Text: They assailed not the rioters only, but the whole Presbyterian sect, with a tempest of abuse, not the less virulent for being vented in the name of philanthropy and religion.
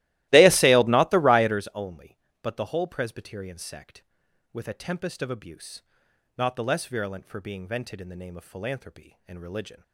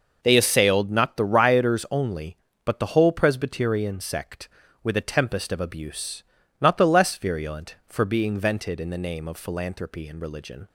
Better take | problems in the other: second | starts louder than the rest; strong; until 1.6 s; 17 dB

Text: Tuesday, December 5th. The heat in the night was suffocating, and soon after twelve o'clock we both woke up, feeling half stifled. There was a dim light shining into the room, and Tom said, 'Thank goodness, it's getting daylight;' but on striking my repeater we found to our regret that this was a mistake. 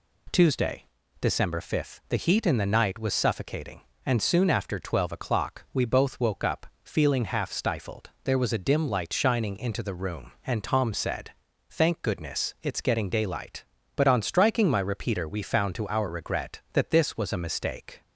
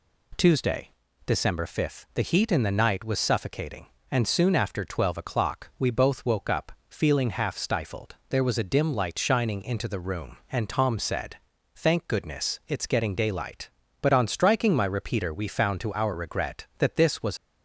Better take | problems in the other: first | stops before "a mistake"; at 17.3 s

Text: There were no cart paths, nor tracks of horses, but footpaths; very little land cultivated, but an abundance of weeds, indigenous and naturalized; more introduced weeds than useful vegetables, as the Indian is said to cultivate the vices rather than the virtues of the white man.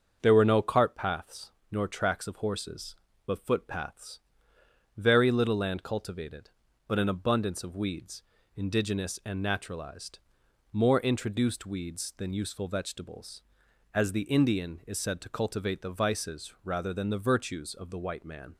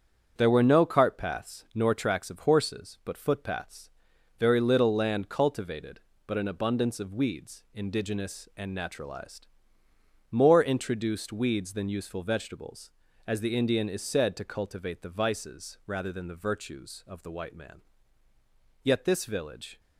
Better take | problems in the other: first | starts louder than the rest; strong; until 1.3 s; 8 dB; also in the first // goes on to say "Yet this village"; noticeable; from 18.8 s on; 0.96 s long

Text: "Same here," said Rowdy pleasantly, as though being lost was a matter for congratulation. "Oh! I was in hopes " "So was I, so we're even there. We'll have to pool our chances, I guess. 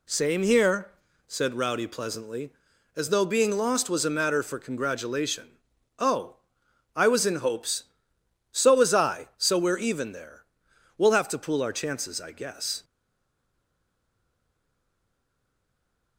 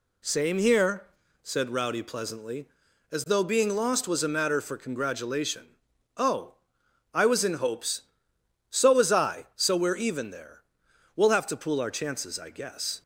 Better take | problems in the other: second | stays silent after the last word; strong; from 12.8 s on; 3.3 s long

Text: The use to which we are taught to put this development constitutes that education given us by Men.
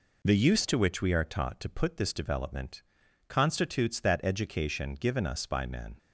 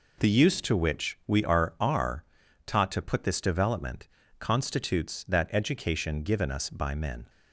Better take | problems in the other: first | says "are" twice; at 1.7 s // pauses between "development" and "constitutes"; slight; at 4.0 s; 0.32 s long; also in the first

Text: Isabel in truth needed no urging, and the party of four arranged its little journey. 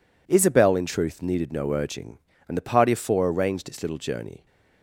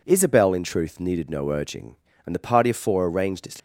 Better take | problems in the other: first | stops before "little journey"; at 3.5 s

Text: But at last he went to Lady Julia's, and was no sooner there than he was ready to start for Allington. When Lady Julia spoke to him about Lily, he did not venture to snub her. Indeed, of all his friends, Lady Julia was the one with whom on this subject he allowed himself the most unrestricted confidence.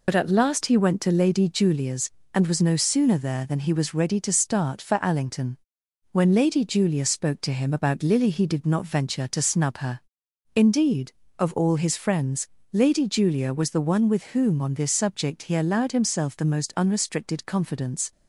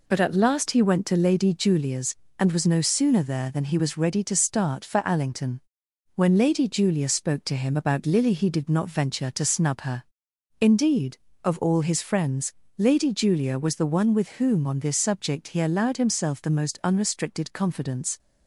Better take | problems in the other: second | loses the start of "But"; at 0.0 s; 50 ms

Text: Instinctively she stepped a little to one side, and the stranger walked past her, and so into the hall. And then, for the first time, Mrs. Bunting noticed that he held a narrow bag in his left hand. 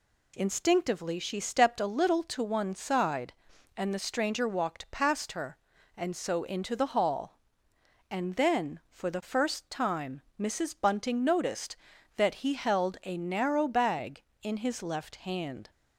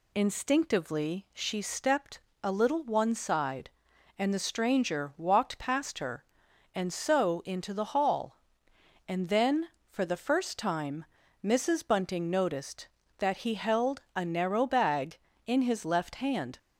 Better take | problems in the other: first | pauses between "stepped" and "a"; slight; at 2.2 s; 0.22 s long // skips "to"; at 2.8 s

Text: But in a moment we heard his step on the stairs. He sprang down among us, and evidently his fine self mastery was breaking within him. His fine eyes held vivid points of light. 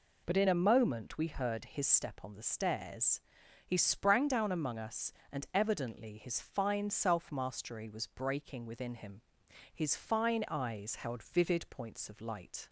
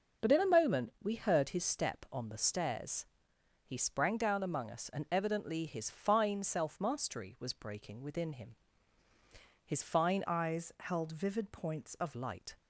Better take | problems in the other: first | changes voice from "eyes" to "of"; from 10.2 to 12.1 s; 1.9 s long

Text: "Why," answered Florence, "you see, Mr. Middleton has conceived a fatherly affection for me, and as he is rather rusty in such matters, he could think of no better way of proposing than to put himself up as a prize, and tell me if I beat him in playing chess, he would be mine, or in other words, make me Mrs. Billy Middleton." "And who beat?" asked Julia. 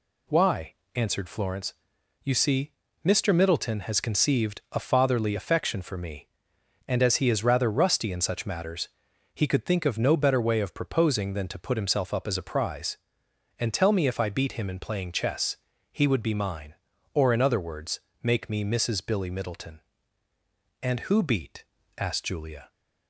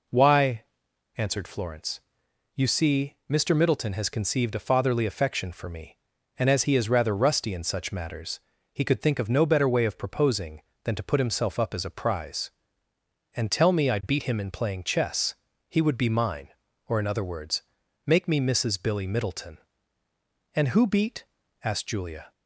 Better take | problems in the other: first | skips "if"; at 13.8 s

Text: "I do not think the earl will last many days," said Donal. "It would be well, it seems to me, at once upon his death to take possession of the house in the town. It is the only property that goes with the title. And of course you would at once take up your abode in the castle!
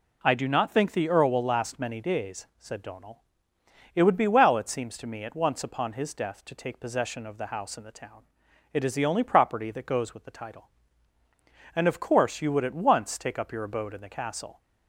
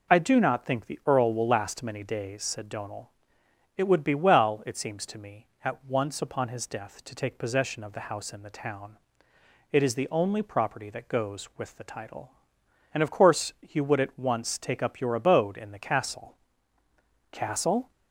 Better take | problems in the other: first | says "castle" twice; at 17.3 s

